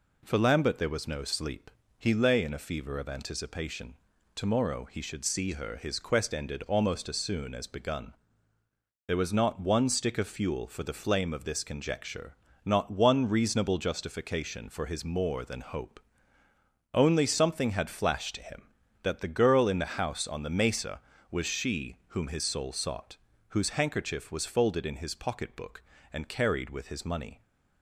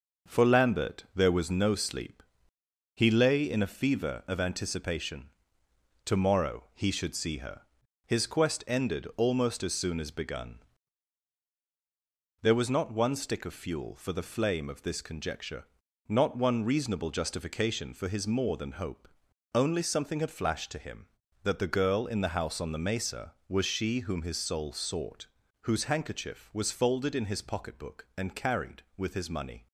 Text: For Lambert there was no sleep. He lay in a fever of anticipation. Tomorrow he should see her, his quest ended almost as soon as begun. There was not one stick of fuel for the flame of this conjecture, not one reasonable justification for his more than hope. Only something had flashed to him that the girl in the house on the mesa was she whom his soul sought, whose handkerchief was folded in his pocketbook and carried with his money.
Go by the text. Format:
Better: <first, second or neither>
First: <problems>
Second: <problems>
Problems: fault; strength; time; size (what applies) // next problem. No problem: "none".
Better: first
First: none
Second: gets quieter; noticeable; throughout; 5.5 dB